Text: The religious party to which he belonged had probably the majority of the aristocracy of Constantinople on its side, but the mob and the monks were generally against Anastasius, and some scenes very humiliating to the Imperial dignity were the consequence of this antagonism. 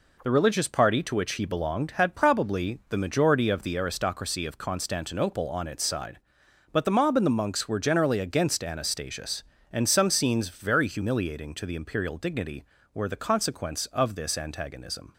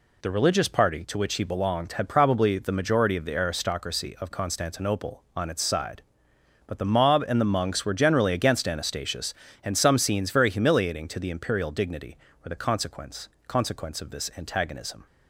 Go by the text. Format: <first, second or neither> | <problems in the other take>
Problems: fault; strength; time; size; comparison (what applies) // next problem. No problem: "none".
first | says "consequence" twice; at 13.4 s